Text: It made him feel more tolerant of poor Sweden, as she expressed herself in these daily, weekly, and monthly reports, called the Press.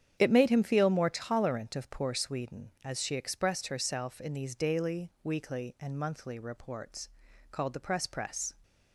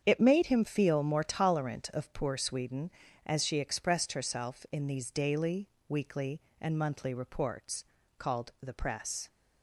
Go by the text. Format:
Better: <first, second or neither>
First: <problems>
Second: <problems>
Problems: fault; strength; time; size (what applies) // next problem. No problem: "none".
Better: second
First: starts louder than the rest; strong; until 1.2 s; 9 dB // says "Press" twice; at 8.0 s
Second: starts louder than the rest; strong; until 1.0 s; 7.5 dB